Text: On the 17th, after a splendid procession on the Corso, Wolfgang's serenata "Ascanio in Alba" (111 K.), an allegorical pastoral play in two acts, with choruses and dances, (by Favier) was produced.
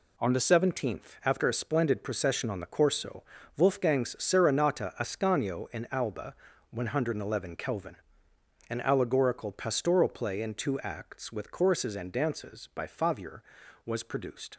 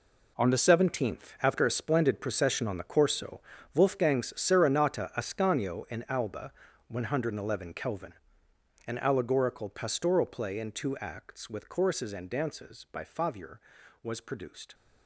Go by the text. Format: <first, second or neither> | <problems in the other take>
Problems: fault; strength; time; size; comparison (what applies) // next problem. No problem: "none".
first | gets quieter; strong; throughout; 12.5 dB